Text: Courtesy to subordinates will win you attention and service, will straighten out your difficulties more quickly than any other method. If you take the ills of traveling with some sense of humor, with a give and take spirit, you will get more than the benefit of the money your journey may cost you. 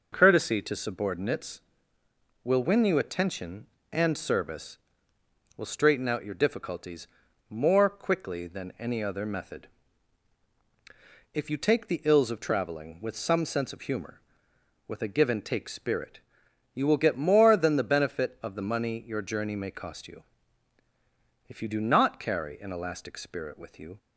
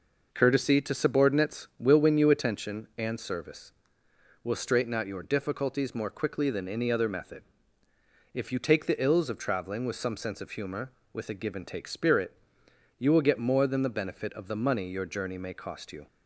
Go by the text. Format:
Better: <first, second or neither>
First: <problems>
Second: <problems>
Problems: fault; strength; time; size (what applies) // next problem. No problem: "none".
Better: second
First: pauses between "difficulties" and "more"; at 7.0 s; 0.42 s long // goes on to say "If you do not carry an elastic spirit with you"; strong; from 21.4 s on; 2.5 s long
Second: none